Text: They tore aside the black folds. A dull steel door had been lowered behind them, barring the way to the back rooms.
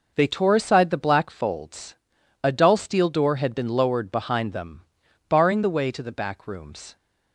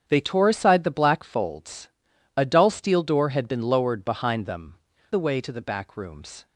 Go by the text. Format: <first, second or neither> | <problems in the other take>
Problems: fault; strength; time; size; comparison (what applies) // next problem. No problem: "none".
first | starts louder than the rest; strong; until 1.0 s; 8 dB // skips "barring"; at 4.9 s